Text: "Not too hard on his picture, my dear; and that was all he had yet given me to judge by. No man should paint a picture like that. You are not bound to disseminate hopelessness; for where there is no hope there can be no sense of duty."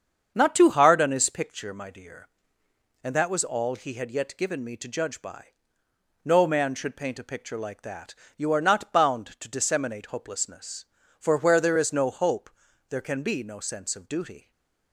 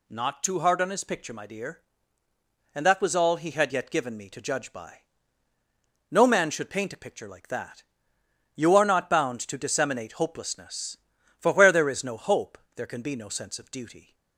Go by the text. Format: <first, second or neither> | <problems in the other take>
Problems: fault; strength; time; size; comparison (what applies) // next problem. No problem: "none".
second | starts louder than the rest; strong; until 1.4 s; 7.5 dB // pauses between "hope" and "there"; at 12.4 s; 0.40 s long; slight in the second // stays silent after the last word; slight; from 14.3 s on; 0.6 s long